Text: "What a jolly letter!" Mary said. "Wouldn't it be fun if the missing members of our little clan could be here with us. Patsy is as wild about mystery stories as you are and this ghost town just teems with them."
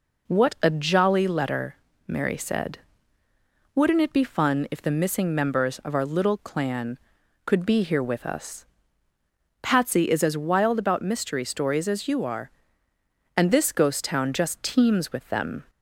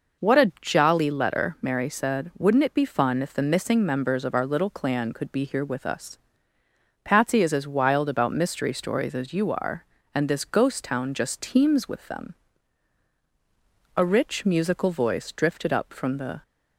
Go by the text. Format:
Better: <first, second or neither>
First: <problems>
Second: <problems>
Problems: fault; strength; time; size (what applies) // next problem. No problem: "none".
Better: first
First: none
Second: goes on to say "A rich musical voice drifted up from the"; strong; from 13.9 s on; 2.4 s long